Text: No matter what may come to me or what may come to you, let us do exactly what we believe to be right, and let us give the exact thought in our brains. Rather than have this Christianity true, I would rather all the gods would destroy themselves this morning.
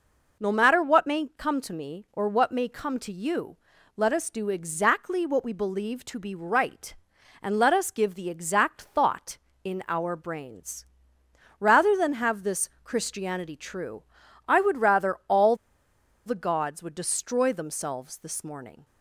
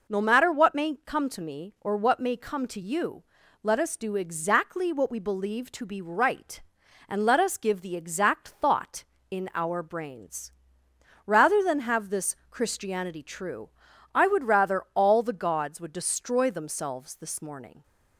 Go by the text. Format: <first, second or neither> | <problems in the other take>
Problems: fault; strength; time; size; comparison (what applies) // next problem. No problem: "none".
second | pauses between "all" and "the"; noticeable; at 15.5 s; 0.71 s long